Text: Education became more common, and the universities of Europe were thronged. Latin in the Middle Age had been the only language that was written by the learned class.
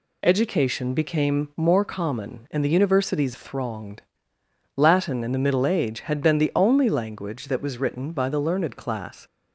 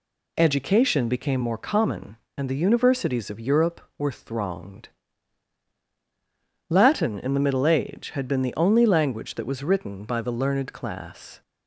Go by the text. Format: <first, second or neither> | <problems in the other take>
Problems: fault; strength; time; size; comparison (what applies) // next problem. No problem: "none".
second | skips "of Europe were"; at 3.3 s